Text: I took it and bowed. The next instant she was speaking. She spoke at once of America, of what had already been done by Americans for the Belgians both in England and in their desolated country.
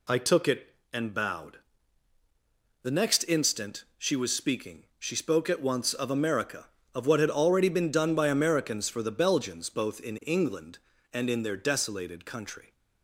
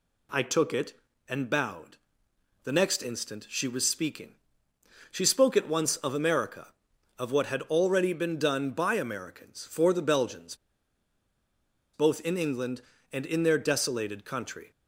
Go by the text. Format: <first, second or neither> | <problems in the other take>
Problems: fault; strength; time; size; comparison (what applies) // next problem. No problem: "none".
first | pauses between "Belgians" and "both"; strong; at 10.5 s; 1.3 s long